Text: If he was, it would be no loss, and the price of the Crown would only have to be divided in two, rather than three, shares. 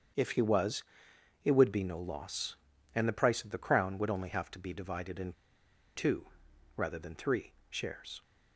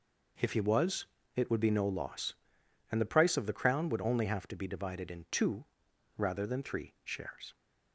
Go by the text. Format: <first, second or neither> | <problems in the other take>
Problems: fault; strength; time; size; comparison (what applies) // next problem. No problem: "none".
second | starts louder than the rest; strong; until 1.7 s; 7.5 dB // pauses between "in" and "two"; noticeable; at 5.3 s; 0.63 s long